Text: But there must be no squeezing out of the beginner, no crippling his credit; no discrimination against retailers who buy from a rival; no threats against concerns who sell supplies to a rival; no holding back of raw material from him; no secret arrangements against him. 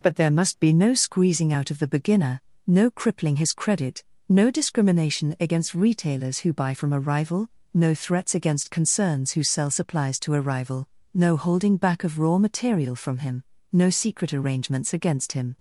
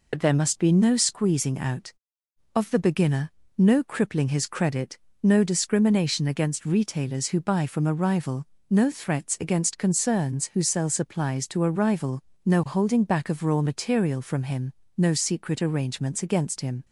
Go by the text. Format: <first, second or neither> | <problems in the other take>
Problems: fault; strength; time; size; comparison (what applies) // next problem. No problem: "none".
first | loses the start of "But"; at 0.1 s; 60 ms